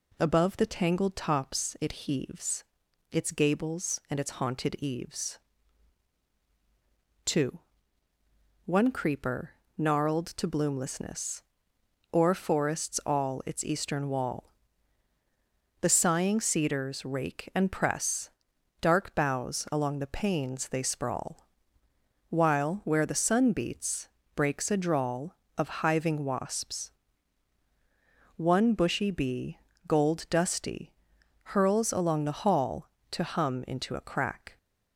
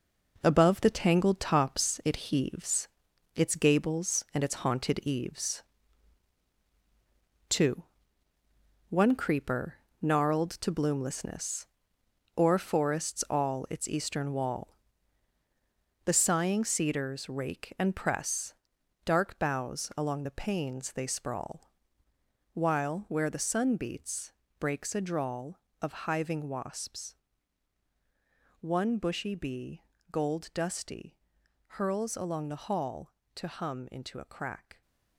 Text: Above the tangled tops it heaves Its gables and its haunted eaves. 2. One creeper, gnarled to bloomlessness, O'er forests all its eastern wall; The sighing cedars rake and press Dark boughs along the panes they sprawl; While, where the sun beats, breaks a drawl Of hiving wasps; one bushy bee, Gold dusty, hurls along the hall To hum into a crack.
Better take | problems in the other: first | gets quieter; strong; throughout; 9 dB // pauses between "heaves" and "Its"; noticeable; at 2.8 s; 0.46 s long; noticeable in the first // pauses between "press" and "Dark"; noticeable; at 18.5 s; 0.52 s long; noticeable in the first

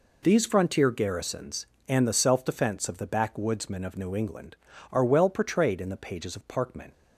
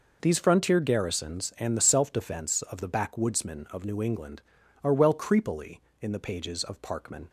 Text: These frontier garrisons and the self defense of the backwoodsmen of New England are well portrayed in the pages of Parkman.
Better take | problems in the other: first | says "creepily" for "portrayed"; at 5.1 s

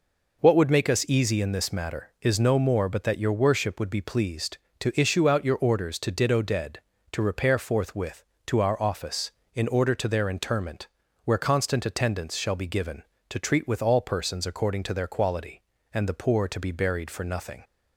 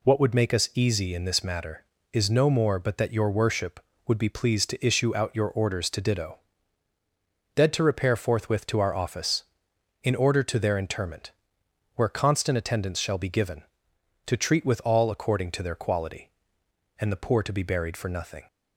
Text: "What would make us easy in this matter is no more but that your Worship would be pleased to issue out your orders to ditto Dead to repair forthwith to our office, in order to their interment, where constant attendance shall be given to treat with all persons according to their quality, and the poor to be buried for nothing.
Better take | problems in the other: first | pauses between "ditto" and "Dead"; at 6.3 s; 1.1 s long // skips "persons"; at 15.1 s

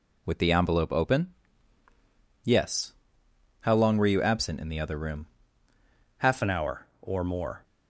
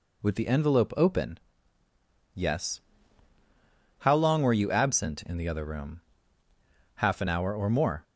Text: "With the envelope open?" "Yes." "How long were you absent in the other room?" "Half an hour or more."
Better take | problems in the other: second | changes voice at "an"; from 6.4 s on; 1.2 s long

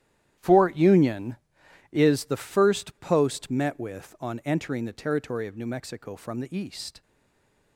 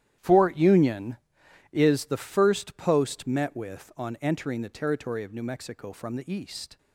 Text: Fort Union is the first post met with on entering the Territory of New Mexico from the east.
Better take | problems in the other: second | starts louder than the rest; strong; until 1.9 s; 11.5 dB; strong in the second // stays silent after the last word; slight; from 7.0 s on; 0.7 s long

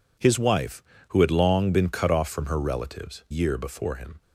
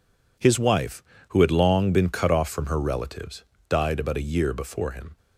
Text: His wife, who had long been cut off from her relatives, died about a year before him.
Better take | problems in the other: second | skips "died about a"; at 3.2 s

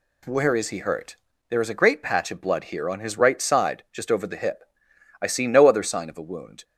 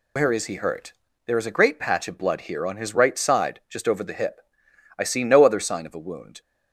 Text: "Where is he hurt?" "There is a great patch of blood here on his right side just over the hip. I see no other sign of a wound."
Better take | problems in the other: first | loses the start of "Where"; at 0.1 s; 160 ms

